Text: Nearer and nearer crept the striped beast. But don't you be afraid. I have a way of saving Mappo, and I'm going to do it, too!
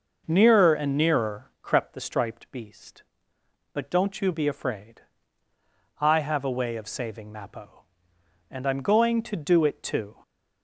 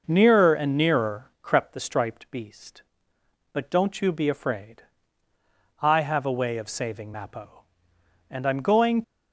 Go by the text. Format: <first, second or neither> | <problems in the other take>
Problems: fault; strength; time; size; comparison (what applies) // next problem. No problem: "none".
first | stops before "to do it too"; at 9.0 s